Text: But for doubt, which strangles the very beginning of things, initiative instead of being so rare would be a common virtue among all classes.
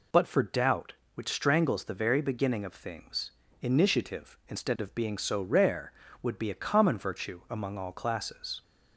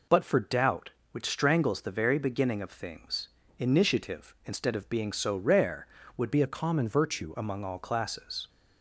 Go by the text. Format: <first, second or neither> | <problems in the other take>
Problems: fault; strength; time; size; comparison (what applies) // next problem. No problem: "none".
first | changes voice from "be" to "virtue"; from 6.3 to 7.3 s; 1.0 s long